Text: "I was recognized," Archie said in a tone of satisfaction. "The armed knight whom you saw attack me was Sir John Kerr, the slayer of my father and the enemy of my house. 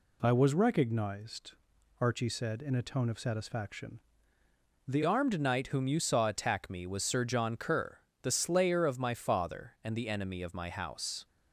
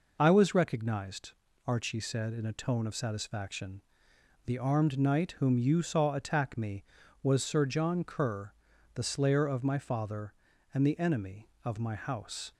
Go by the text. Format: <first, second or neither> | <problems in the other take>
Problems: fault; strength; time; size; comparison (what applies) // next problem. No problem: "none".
second | changes voice at "armed"; from 5.0 s on; 6.2 s long